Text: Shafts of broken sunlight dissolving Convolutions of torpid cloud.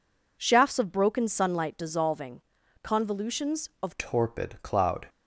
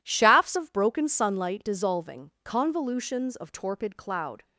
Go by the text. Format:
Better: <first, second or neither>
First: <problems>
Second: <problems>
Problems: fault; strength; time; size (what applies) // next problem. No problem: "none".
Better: second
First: pauses between "dissolving" and "Convolutions"; at 2.4 s; 0.42 s long // changes voice at "torpid"; from 3.9 s on; 1.1 s long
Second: none